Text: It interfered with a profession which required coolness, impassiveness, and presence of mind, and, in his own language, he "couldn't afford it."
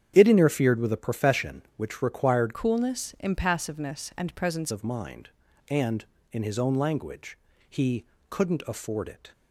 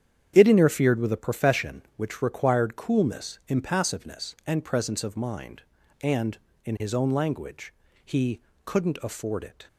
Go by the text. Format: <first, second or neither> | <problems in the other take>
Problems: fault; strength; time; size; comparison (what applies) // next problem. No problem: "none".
second | starts louder than the rest; strong; until 1.1 s; 9 dB; strong in the second // changes voice from "coolness" to "presence"; from 2.5 to 4.7 s; 2.2 s long // pauses between "he" and "couldn't"; slight; at 8.0 s; 0.26 s long; slight in the second